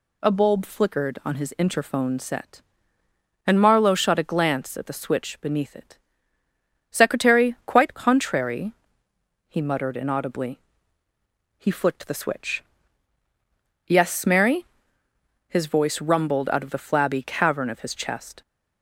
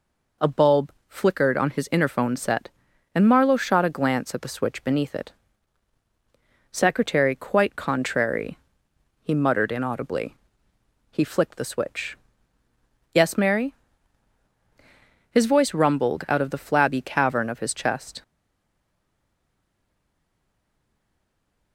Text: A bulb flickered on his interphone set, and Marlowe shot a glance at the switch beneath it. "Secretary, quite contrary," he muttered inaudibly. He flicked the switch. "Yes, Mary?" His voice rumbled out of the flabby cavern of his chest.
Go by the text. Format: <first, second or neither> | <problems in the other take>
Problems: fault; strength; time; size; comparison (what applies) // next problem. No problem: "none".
first | pauses between "bulb" and "flickered"; slight; at 0.9 s; 0.16 s long // stays silent after the last word; strong; from 18.2 s on; 3.5 s long